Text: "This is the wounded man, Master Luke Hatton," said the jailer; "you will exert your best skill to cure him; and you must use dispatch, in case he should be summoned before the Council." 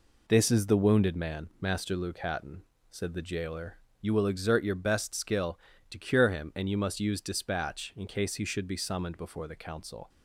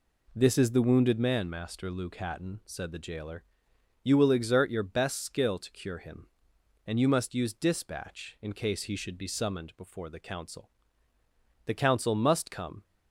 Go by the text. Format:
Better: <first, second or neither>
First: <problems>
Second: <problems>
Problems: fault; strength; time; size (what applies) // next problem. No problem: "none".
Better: first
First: none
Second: goes on to say "The Council must come"; noticeable; from 11.6 s on; 1.1 s long